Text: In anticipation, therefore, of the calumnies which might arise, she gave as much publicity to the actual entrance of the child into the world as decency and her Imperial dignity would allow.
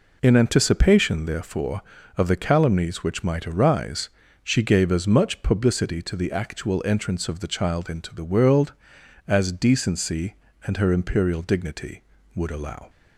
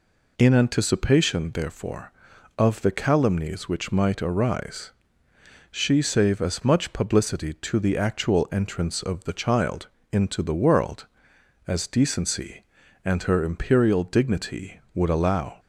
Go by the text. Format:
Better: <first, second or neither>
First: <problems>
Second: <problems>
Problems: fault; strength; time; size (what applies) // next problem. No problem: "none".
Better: first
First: none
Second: says "save" for "gave"; at 6.0 s // pauses between "child" and "into"; slight; at 9.8 s; 0.24 s long